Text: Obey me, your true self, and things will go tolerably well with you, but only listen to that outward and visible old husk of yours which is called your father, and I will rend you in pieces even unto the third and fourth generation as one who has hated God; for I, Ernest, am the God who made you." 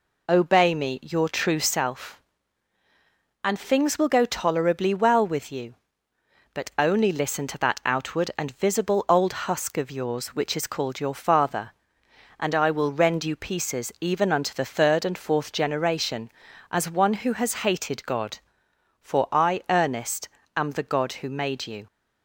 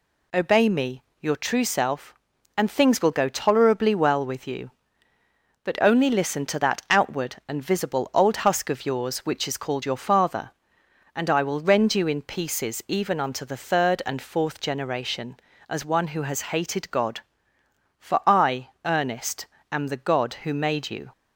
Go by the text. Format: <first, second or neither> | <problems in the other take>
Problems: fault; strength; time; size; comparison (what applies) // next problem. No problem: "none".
second | skips "in"; at 13.3 s